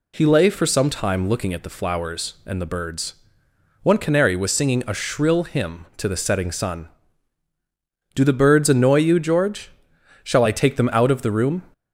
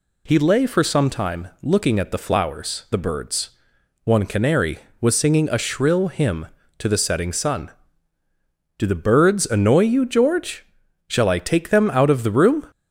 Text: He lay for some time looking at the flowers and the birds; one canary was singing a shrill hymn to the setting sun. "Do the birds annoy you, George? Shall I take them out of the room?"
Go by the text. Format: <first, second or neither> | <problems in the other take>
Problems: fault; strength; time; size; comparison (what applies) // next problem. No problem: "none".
first | pauses between "time" and "looking"; slight; at 1.4 s; 0.16 s long // skips "and"; at 2.8 s